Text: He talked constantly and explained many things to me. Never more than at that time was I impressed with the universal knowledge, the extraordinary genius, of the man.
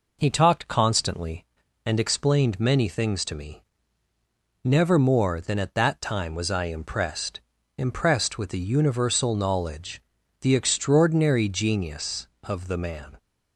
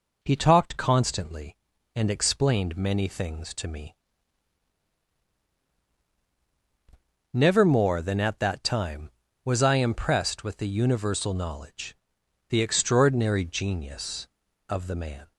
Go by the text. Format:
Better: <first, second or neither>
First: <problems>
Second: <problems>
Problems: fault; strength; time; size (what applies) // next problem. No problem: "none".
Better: second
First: says "impressed" twice; at 7.7 s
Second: none